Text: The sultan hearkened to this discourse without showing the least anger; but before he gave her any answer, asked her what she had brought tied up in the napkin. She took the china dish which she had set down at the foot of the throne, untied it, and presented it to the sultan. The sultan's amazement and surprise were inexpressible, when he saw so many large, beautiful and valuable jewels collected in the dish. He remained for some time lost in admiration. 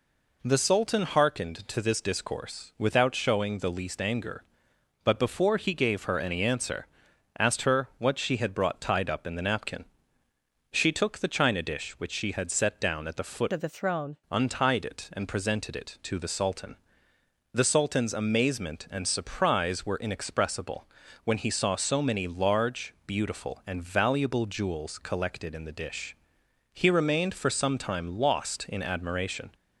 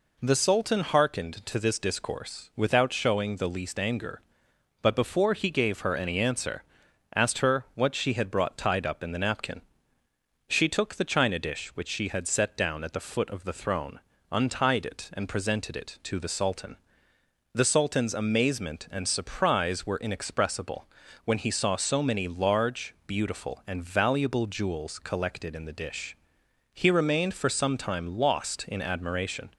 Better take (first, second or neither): second